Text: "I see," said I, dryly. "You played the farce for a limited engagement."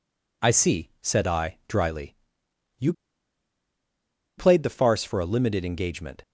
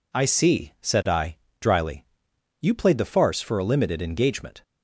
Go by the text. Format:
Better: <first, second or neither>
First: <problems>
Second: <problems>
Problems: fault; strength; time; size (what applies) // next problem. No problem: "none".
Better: second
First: pauses between "You" and "played"; strong; at 2.9 s; 1.4 s long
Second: none